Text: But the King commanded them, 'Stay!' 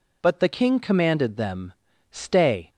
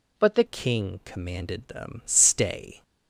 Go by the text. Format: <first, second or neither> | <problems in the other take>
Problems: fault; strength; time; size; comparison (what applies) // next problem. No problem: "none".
first | changes voice at "King"; from 0.4 s on; 2.4 s long